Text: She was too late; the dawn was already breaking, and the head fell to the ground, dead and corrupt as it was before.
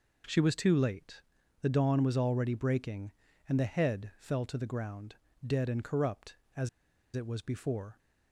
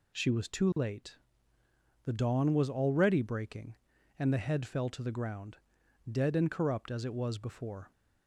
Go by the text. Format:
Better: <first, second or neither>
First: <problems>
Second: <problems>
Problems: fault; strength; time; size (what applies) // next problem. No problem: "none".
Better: second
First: pauses between "as" and "it"; noticeable; at 6.6 s; 0.46 s long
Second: none